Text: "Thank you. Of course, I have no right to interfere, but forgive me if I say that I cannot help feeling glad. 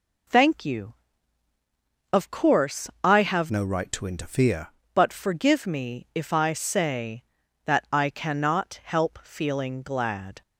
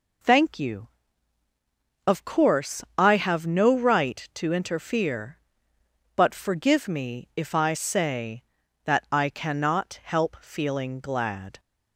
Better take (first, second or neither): second